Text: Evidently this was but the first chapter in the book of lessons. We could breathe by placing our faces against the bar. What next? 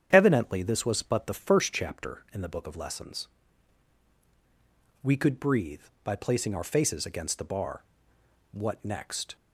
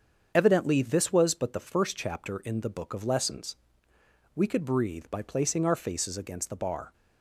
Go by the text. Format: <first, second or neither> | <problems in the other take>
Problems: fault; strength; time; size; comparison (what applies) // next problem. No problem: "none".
first | starts louder than the rest; strong; until 1.3 s; 7.5 dB; strong in the first // stops before "What next"; at 6.9 s